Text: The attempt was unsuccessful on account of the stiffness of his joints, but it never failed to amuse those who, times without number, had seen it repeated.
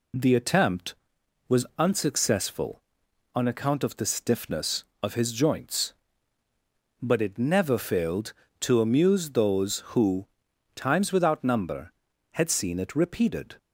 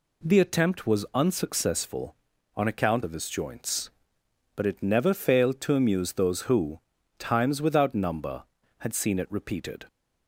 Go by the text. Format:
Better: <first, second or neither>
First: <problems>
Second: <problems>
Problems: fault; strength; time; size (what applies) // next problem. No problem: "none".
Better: first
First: none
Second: skips "of the stiffness"; at 3.0 s